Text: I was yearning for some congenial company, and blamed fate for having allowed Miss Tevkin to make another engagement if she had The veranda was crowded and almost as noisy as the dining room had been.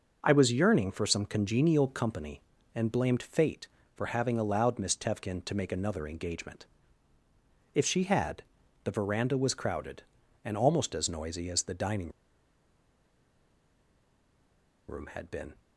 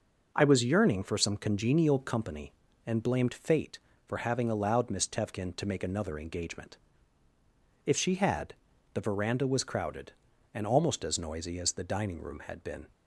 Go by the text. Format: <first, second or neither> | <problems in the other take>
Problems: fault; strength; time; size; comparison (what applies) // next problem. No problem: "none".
second | pauses between "engagement" and "if"; at 6.6 s; 1.0 s long; also in the second // pauses between "had" and "The"; at 8.4 s; 0.42 s long; also in the second // pauses between "dining" and "room"; strong; at 12.1 s; 2.7 s long